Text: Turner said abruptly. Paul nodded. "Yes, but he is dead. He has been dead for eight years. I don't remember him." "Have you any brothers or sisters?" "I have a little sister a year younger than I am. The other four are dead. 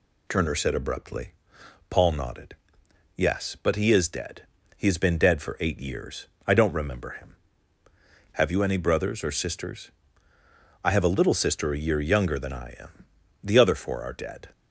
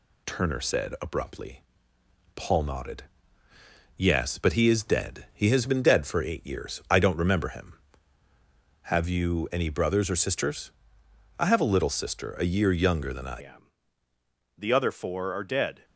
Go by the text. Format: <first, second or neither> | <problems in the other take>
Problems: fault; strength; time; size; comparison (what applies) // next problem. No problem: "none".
first | changes voice at "am"; from 13.4 s on; 2.4 s long